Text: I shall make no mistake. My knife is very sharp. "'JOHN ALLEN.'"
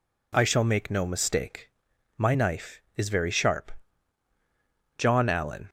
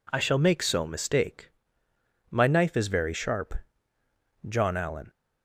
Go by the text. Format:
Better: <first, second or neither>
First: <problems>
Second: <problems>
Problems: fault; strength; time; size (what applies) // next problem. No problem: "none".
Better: first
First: none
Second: says "so" for "no"; at 0.6 s